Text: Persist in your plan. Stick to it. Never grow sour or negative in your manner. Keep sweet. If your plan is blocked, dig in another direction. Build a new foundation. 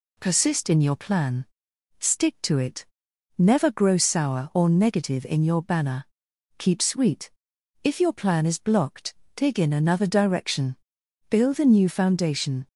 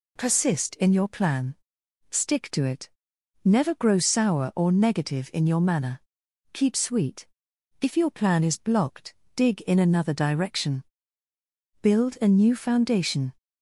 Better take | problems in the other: second | says "banner" for "manner"; at 5.6 s

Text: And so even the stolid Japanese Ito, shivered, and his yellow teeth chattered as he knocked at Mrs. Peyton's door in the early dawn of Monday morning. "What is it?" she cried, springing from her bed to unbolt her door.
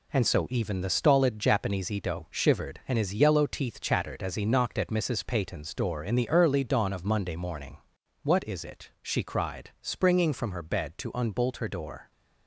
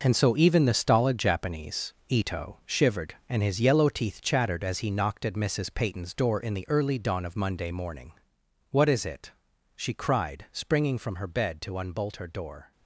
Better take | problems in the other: first | gets quieter; strong; throughout; 10 dB

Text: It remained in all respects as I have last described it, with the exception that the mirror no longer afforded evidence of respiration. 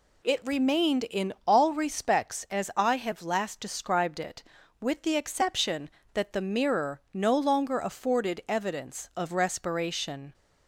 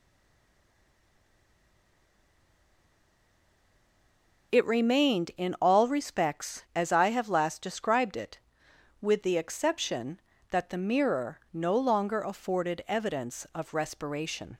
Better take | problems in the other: first | stays silent before the first word; strong; until 4.5 s; 4.5 s long

